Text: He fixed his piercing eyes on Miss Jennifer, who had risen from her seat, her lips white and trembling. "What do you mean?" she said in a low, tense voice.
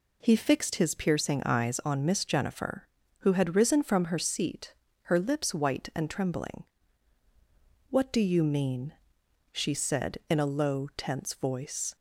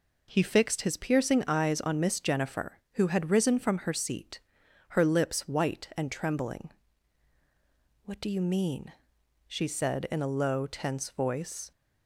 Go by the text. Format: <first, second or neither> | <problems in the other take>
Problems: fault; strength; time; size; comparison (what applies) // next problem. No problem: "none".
neither | none